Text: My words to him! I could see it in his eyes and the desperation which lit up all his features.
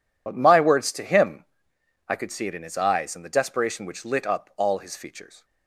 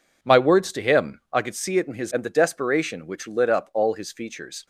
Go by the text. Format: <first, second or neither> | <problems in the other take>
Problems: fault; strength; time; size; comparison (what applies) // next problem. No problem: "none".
first | skips "eyes"; at 2.1 s